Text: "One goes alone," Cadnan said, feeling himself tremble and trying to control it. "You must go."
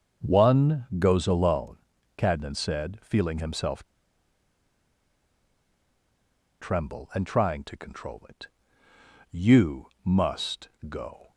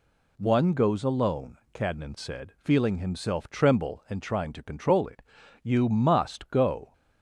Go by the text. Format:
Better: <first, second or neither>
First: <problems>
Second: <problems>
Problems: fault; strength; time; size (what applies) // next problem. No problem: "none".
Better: second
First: starts louder than the rest; until 1.3 s; 6.5 dB // pauses between "himself" and "tremble"; strong; at 3.8 s; 2.7 s long // pauses between "You" and "must"; slight; at 9.8 s; 0.18 s long // pauses between "must" and "go"; slight; at 10.6 s; 0.20 s long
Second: none